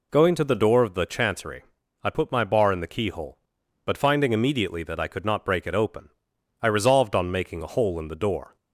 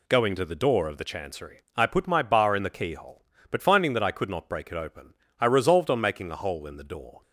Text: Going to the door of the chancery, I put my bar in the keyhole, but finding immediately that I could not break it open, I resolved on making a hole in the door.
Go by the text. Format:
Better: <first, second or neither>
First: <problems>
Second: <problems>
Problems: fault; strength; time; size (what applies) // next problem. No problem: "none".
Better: first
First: none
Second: skips "immediately"; at 3.9 s